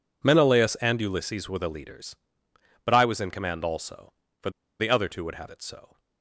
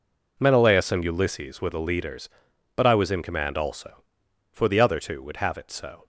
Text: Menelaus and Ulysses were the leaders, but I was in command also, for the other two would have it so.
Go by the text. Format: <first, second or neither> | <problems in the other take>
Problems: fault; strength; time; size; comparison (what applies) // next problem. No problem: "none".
second | pauses between "for" and "the"; slight; at 4.5 s; 0.28 s long